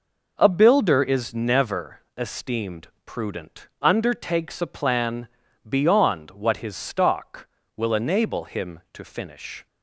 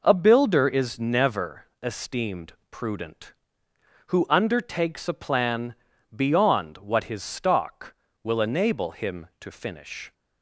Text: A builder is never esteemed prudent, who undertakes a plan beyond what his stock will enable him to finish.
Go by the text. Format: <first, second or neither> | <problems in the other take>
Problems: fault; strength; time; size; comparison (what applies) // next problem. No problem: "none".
second | pauses between "never" and "esteemed"; slight; at 2.0 s; 0.18 s long; slight in the second // pauses between "esteemed" and "prudent"; slight; at 2.8 s; 0.18 s long; slight in the second // skips "who"; at 3.7 s // pauses between "plan" and "beyond"; at 5.2 s; 0.40 s long; also in the second